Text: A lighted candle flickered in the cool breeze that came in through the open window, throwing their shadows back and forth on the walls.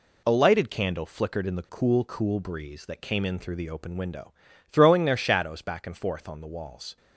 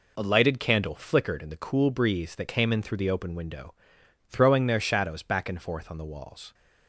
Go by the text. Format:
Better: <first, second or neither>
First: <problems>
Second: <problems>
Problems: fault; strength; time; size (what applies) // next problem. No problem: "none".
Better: second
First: says "cool" twice; at 2.0 s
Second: none